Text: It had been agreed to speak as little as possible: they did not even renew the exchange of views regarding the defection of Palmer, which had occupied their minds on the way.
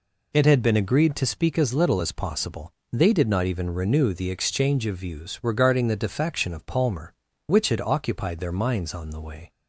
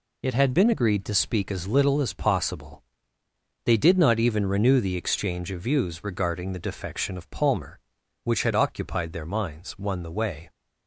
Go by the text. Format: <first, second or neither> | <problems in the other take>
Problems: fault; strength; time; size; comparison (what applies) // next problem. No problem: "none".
first | says "one" for "on"; at 9.7 s